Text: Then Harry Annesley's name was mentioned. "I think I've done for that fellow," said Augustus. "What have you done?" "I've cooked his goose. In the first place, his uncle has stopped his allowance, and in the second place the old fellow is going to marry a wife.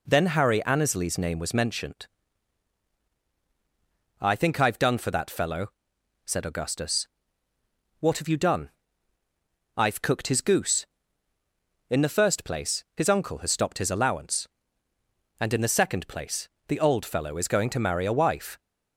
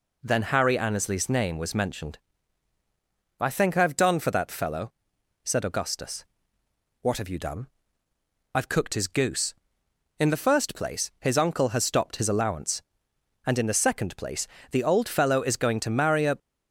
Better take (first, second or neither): first